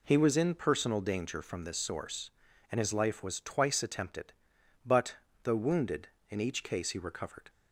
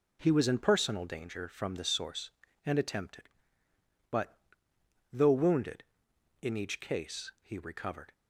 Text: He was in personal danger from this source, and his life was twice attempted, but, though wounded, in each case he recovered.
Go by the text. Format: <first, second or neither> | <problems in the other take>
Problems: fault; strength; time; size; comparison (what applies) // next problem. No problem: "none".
first | skips "his life was twice"; at 2.7 s